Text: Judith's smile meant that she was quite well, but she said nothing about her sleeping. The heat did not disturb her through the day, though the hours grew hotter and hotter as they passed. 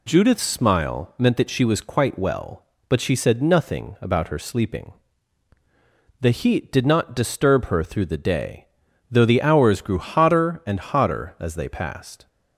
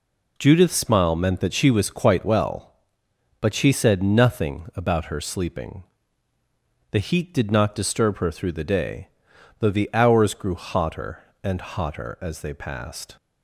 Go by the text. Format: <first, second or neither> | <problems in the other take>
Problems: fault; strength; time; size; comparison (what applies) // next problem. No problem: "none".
neither | none